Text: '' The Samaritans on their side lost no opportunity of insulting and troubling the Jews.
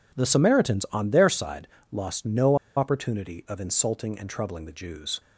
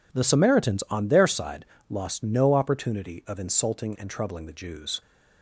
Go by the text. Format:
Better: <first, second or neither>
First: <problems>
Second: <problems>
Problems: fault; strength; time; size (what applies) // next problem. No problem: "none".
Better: second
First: pauses between "side" and "lost"; slight; at 1.6 s; 0.24 s long // pauses between "no" and "opportunity"; slight; at 2.5 s; 0.21 s long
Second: pauses between "side" and "lost"; slight; at 1.6 s; 0.24 s long